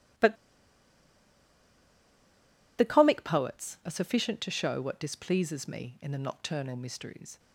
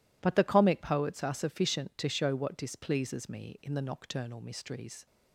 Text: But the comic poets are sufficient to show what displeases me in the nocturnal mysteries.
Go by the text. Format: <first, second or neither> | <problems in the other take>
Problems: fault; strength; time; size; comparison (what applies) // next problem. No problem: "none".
second | pauses between "But" and "the"; strong; at 0.3 s; 2.4 s long